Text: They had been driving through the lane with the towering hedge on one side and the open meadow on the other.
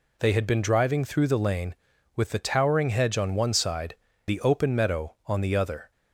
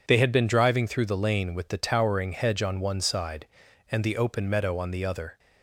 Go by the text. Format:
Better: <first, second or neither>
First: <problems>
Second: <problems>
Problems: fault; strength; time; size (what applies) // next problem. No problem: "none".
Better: second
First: skips "and"; at 4.1 s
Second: none